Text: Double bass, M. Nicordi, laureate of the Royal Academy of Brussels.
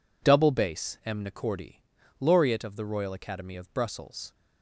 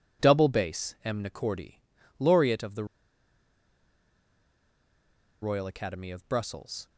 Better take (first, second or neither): first